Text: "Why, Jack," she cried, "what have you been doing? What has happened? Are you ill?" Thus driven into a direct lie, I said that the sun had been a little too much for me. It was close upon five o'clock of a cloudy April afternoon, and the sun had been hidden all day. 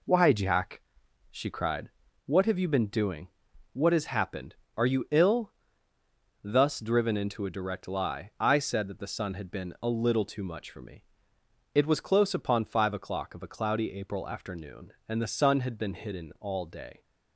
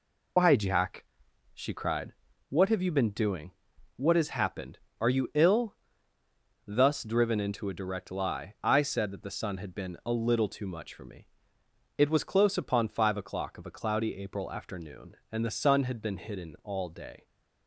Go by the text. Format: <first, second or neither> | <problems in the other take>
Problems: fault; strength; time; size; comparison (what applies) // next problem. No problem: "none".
first | loses the start of "Why"; at 0.3 s; 90 ms